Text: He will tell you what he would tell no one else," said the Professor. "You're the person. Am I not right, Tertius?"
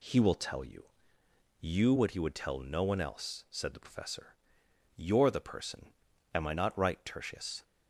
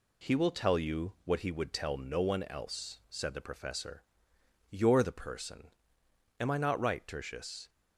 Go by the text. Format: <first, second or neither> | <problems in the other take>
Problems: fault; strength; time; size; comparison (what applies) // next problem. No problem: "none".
second | says "you" twice; at 1.6 s